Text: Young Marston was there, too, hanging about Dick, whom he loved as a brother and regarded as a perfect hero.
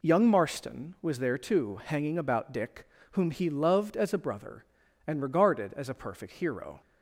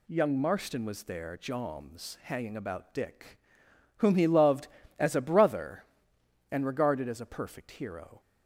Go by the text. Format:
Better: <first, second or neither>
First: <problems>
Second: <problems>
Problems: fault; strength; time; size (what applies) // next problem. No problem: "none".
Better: first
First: none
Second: says "joms" for "too"; at 1.3 s